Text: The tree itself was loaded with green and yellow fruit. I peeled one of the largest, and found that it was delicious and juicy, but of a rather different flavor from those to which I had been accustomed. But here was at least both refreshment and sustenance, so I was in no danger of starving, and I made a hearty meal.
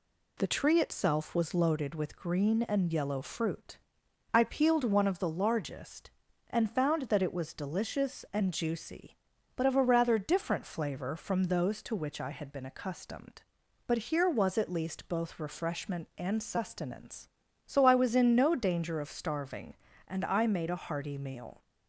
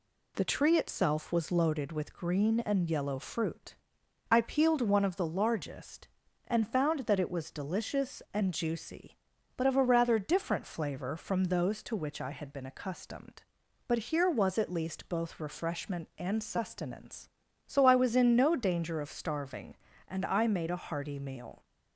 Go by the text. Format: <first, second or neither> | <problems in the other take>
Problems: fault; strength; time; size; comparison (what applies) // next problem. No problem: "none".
neither | none